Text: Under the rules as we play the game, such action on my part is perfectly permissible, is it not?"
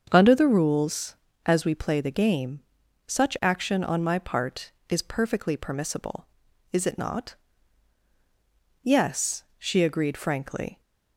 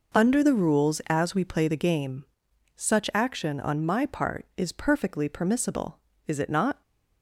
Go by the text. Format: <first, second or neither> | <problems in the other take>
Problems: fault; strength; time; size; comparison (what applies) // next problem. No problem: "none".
second | starts louder than the rest; until 1.1 s; 7 dB // goes on to say "Yes she agreed frankly"; strong; from 8.8 s on; 1.9 s long